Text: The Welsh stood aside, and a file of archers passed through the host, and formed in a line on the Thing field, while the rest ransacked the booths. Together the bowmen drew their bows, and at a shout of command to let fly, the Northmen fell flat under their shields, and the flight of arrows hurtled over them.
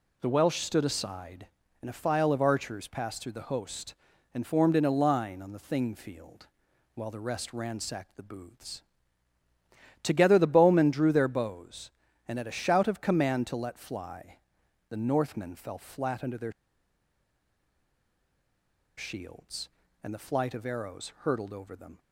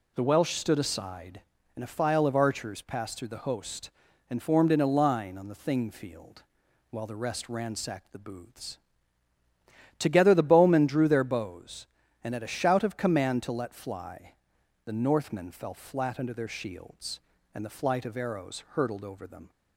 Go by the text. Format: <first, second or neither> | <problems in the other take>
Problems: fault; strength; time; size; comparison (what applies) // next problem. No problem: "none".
second | pauses between "their" and "shields"; strong; at 16.5 s; 2.4 s long